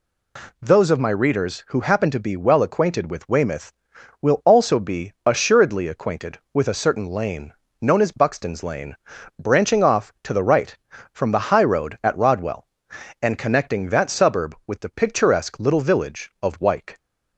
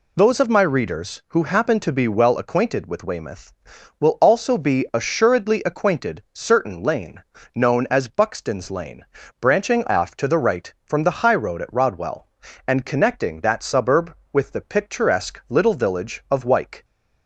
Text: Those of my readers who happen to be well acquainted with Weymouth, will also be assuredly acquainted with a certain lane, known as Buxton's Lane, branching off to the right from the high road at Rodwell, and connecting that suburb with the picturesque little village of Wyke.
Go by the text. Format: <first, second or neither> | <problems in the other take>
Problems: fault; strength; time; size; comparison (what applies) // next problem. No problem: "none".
first | skips "with a"; at 6.2 s